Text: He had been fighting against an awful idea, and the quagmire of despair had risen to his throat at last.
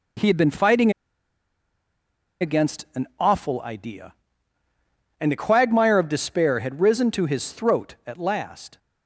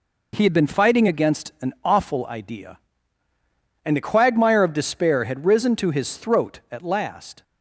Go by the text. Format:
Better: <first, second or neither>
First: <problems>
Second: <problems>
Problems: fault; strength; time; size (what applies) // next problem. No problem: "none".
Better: second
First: pauses between "fighting" and "against"; strong; at 0.8 s; 1.5 s long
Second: none